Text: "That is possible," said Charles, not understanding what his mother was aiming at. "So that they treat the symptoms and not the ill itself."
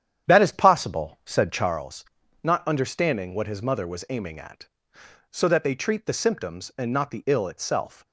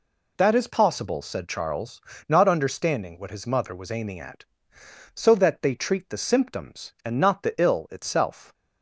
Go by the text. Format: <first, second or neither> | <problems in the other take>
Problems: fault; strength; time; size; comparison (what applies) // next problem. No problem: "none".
second | starts louder than the rest; strong; until 1.8 s; 9.5 dB